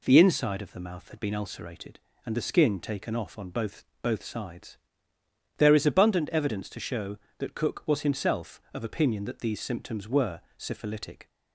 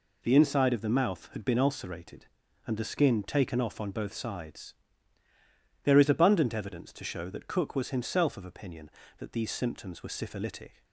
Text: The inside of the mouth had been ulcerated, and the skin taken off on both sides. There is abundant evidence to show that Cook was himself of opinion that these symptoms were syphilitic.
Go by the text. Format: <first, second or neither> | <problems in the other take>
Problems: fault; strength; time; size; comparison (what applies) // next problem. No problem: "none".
second | says "both" twice; at 4.0 s // pauses between "were" and "syphilitic"; slight; at 10.4 s; 0.18 s long